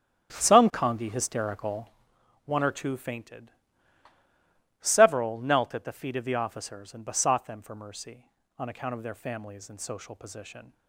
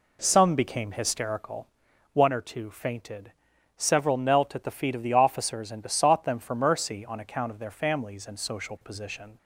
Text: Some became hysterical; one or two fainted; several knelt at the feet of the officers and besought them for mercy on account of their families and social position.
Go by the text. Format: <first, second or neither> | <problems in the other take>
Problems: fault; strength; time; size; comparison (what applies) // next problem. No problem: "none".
second | starts louder than the rest; strong; until 1.3 s; 10 dB // says "congi" for "became"; at 0.7 s